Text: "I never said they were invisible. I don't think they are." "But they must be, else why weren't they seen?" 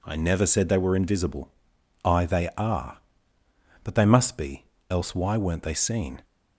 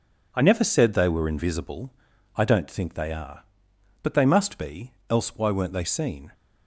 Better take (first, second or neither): second